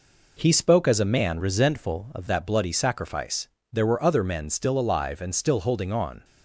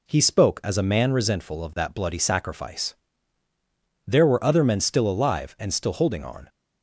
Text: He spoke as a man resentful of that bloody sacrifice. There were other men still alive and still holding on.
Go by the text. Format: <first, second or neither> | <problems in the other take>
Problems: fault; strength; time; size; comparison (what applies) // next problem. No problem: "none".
second | changes voice from "resentful" to "of"; from 1.3 to 2.2 s; 0.9 s long